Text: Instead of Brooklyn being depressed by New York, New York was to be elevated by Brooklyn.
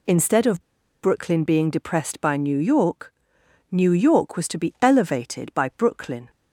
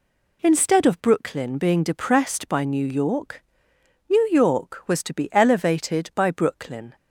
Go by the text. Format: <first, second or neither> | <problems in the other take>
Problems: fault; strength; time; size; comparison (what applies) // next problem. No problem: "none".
second | pauses between "of" and "Brooklyn"; at 0.6 s; 0.42 s long